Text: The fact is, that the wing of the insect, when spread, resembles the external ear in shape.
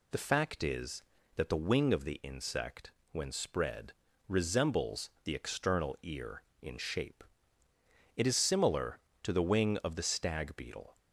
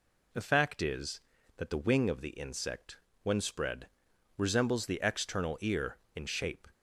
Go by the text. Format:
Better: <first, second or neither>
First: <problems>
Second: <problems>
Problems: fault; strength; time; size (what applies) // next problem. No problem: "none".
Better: second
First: goes on to say "It is similar to the wing of the stag beetle"; strong; from 8.1 s on; 2.8 s long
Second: none